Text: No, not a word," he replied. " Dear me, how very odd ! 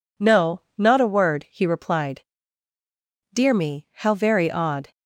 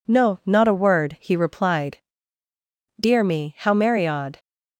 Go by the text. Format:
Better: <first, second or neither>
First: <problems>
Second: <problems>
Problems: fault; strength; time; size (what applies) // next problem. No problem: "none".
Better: first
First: none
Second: says "merry" for "very"; at 3.7 s